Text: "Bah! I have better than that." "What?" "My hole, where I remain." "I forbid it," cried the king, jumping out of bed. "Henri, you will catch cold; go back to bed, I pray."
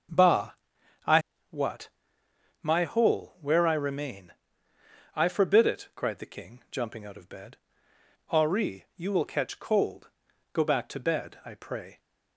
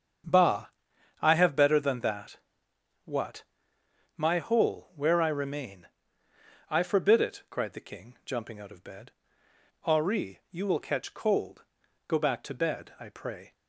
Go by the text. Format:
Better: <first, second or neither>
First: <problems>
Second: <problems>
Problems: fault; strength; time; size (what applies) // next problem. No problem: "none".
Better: second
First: starts louder than the rest; until 2.6 s; 6.5 dB // skips "have better than that"; at 1.3 s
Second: starts louder than the rest; strong; until 1.7 s; 7.5 dB